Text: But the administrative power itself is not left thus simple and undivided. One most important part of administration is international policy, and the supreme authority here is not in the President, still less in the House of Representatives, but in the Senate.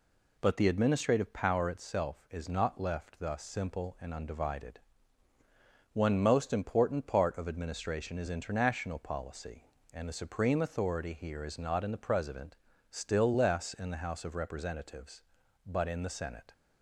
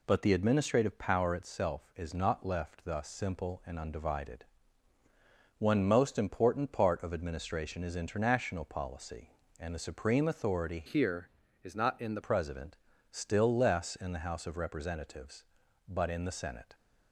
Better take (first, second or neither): first